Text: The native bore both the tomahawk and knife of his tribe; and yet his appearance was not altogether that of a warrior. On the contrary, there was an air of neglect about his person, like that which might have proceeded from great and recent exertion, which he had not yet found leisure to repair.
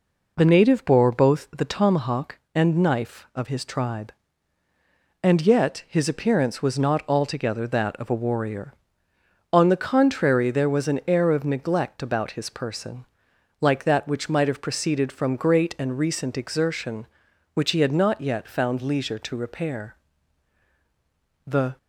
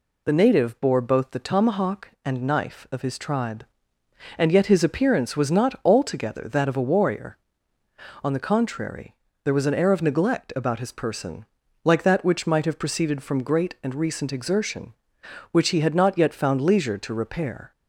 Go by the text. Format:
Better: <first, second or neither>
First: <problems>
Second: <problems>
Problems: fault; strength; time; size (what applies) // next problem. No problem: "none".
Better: second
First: goes on to say "The"; slight; from 21.4 s on; 0.30 s long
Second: none